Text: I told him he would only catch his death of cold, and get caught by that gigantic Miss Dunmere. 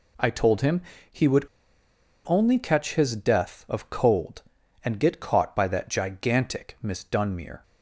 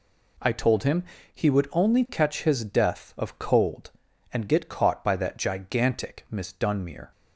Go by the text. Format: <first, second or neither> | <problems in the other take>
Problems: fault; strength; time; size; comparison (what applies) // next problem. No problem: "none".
second | pauses between "him" and "he"; slight; at 0.8 s; 0.30 s long; slight in the second // pauses between "would" and "only"; noticeable; at 1.4 s; 0.80 s long